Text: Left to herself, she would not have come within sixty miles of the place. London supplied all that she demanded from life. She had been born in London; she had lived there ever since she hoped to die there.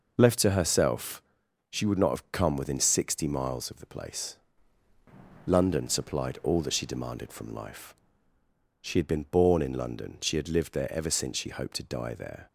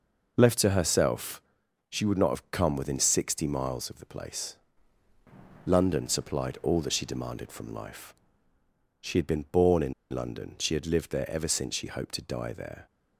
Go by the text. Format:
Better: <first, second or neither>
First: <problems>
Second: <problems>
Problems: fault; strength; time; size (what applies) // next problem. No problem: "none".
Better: first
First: none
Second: pauses between "in" and "London"; slight; at 9.9 s; 0.18 s long